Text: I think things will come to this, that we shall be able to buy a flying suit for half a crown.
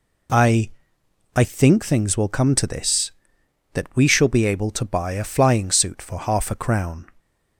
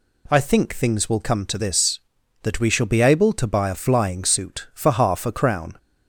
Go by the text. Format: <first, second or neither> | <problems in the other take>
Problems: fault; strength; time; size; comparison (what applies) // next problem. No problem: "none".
second | says "I" twice; at 1.3 s